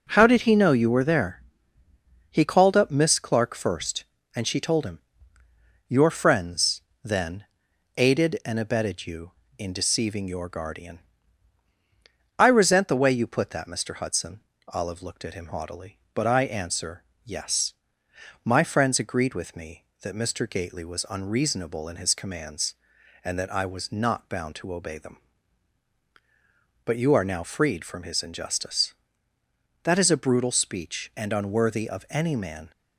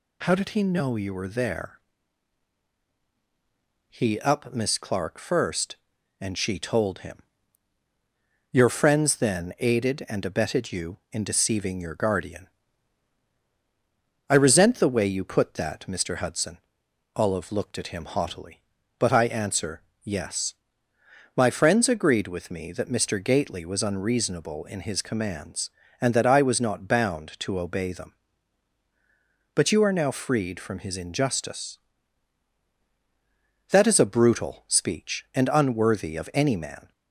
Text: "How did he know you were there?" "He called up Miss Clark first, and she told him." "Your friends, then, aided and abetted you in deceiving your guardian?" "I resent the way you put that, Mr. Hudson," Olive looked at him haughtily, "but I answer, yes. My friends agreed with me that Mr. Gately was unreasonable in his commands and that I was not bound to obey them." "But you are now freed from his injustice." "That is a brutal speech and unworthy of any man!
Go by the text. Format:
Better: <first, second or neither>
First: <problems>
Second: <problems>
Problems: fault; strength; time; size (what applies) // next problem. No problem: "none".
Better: first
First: none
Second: skips "called"; at 4.1 s